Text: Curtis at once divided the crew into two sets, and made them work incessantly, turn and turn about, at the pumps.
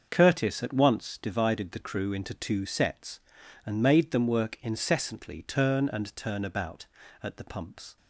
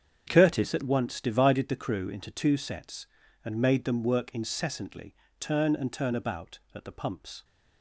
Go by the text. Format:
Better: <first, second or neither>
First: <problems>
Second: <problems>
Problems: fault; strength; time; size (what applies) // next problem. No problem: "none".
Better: neither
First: starts louder than the rest; until 1.1 s; 6.5 dB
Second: starts louder than the rest; strong; until 1.2 s; 7.5 dB